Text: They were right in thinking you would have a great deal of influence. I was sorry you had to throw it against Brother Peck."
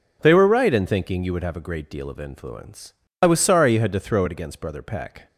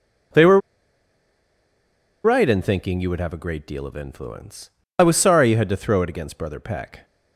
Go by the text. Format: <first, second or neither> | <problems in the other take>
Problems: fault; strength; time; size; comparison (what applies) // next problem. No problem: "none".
first | pauses between "were" and "right"; strong; at 0.5 s; 1.6 s long